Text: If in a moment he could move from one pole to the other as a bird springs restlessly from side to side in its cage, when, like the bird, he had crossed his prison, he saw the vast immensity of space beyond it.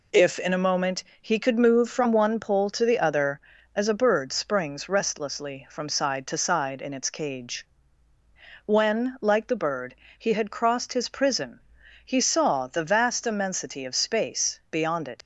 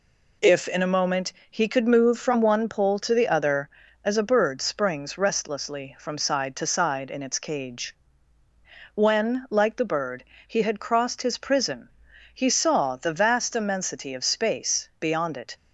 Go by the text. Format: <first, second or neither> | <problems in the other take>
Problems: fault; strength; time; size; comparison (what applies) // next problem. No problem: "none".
second | pauses between "moment" and "he"; slight; at 1.0 s; 0.18 s long; slight in the second // leaves "it" unfinished; at 15.2 s; 60 ms